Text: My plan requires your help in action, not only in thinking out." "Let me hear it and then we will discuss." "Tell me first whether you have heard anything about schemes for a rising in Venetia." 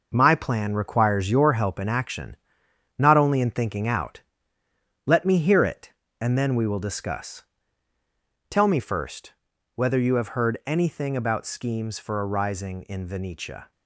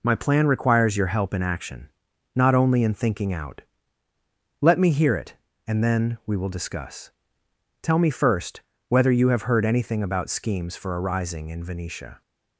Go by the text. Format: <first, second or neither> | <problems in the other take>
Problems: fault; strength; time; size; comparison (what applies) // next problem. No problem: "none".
second | gets quieter; strong; throughout; 8 dB // pauses between "first" and "whether"; at 9.3 s; 0.40 s long; slight in the second